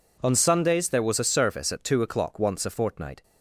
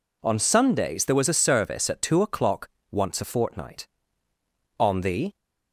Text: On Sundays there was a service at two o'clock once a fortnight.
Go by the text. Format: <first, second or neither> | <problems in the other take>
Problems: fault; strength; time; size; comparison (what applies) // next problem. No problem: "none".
first | pauses between "o'clock" and "once"; slight; at 2.6 s; 0.20 s long // goes on to say "On the"; from 4.7 s on; 0.56 s long